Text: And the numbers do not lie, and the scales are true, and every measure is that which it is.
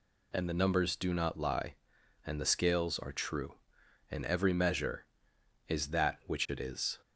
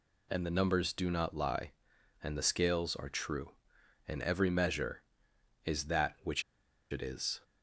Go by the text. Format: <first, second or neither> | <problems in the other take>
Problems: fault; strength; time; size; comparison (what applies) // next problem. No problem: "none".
first | pauses between "which" and "it"; noticeable; at 6.4 s; 0.49 s long